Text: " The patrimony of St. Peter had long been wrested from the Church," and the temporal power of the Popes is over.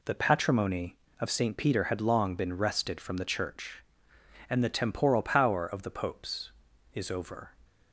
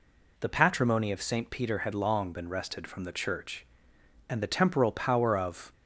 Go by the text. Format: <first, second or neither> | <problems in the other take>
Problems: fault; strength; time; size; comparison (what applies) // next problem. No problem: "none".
first | stops before "the Popes is over"; at 5.7 s